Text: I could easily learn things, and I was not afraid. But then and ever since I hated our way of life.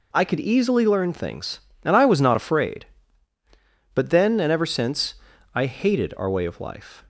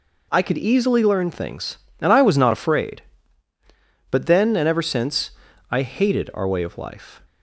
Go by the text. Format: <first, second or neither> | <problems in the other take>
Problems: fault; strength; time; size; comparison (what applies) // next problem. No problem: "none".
neither | pauses between "since" and "I"; the same in both